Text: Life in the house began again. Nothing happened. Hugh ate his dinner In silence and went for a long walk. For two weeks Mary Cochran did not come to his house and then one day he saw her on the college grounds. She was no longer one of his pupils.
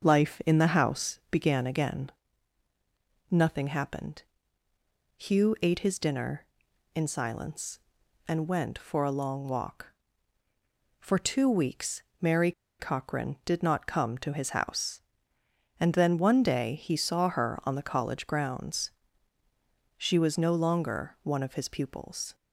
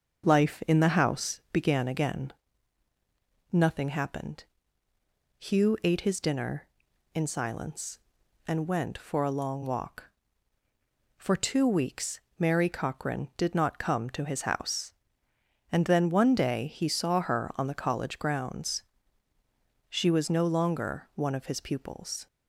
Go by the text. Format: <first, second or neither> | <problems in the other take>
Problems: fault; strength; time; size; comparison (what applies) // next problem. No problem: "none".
second | starts louder than the rest; until 1.0 s; 6 dB; also in the second // pauses between "weeks" and "Mary"; slight; at 12.0 s; 0.18 s long; slight in the second // pauses between "Mary" and "Cochran"; slight; at 12.5 s; 0.28 s long